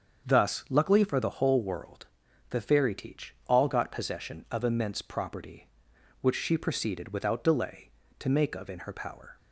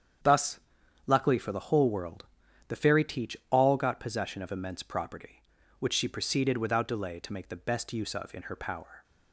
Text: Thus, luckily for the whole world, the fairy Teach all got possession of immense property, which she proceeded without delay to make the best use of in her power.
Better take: second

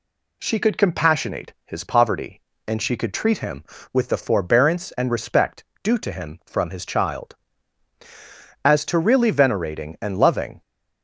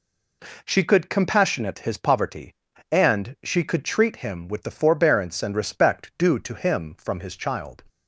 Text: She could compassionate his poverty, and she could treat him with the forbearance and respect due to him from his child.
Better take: second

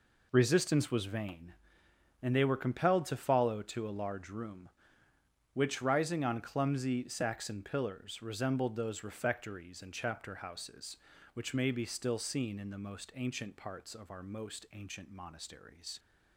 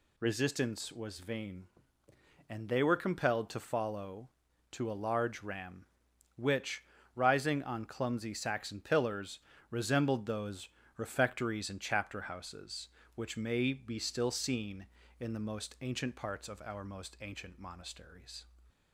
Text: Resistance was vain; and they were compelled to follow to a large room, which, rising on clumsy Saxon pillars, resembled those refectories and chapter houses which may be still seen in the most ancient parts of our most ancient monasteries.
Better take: first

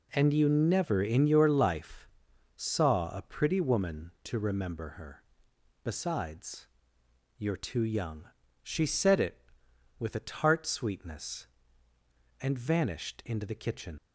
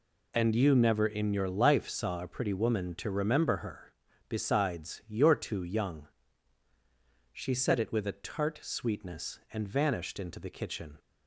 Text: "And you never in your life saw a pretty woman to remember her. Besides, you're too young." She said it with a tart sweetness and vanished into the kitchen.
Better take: second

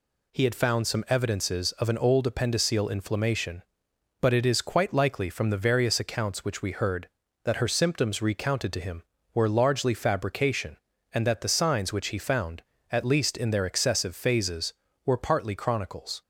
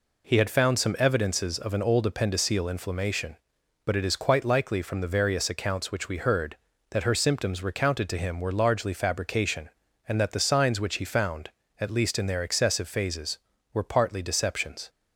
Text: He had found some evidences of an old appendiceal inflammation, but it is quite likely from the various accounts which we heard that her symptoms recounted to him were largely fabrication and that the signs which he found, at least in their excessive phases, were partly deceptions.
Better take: second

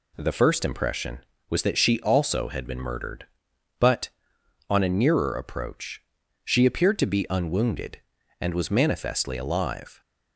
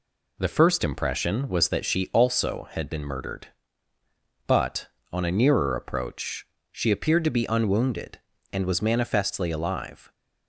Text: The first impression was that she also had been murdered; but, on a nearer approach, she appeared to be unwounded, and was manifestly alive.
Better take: neither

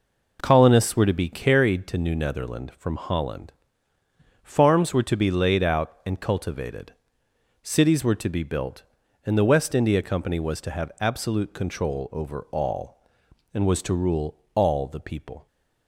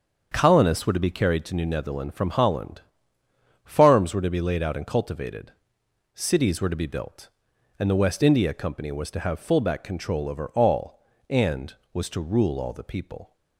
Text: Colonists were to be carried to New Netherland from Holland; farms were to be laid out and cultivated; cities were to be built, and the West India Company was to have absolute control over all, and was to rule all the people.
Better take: first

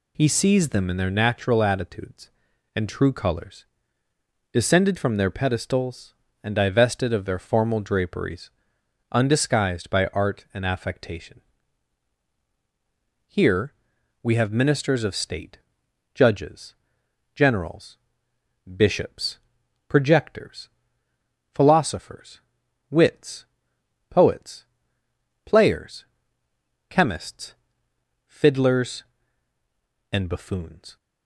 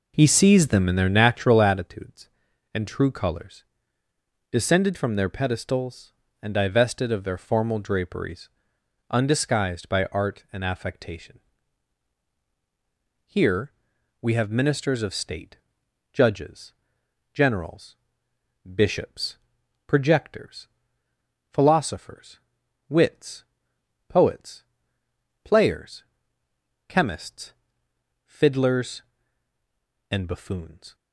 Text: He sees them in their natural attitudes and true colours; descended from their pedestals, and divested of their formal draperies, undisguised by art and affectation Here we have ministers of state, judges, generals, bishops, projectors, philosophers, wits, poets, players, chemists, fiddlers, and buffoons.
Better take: first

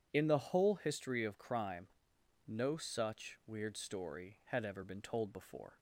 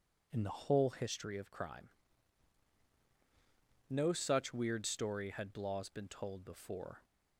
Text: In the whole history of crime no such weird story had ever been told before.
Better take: first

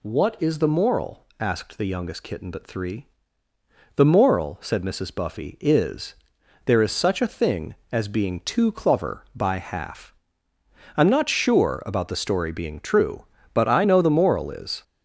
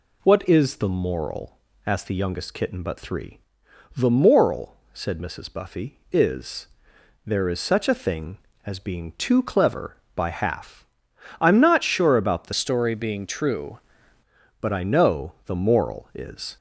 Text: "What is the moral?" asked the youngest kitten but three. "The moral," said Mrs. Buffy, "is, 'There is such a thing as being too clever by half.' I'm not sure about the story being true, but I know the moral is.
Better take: first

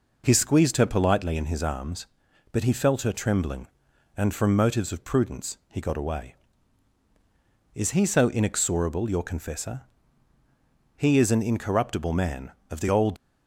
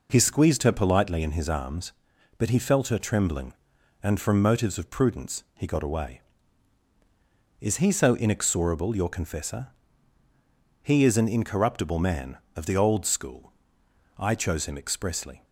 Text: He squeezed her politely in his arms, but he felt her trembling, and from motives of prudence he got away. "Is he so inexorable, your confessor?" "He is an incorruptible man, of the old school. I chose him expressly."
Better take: second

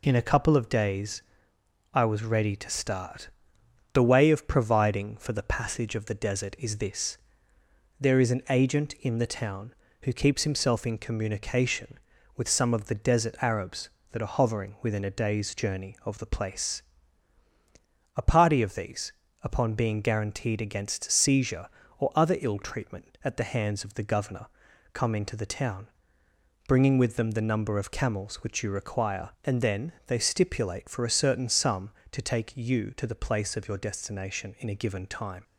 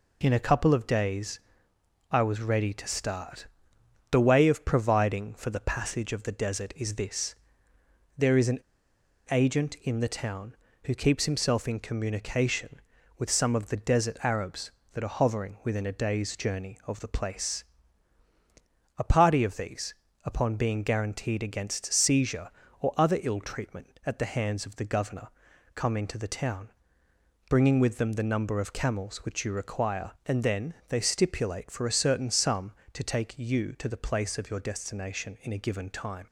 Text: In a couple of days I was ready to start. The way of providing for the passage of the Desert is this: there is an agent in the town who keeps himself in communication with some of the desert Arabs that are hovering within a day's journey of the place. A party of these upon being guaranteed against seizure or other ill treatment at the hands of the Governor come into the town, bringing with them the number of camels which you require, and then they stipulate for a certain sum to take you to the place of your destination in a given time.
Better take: first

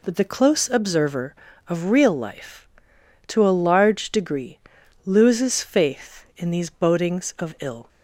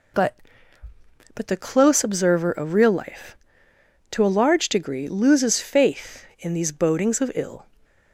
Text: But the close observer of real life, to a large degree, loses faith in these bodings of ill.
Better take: first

